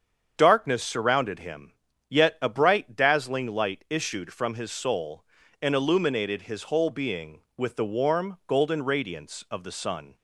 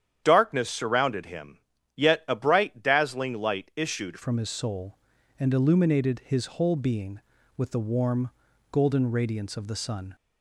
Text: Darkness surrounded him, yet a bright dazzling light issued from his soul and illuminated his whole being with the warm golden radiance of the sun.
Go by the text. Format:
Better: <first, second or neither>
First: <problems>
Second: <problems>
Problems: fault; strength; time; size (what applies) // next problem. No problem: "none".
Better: first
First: starts louder than the rest; strong; until 1.3 s; 7.5 dB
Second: starts louder than the rest; strong; until 1.2 s; 9.5 dB // changes voice at "from"; from 4.2 s on; 5.9 s long // pauses between "warm" and "golden"; at 8.2 s; 0.42 s long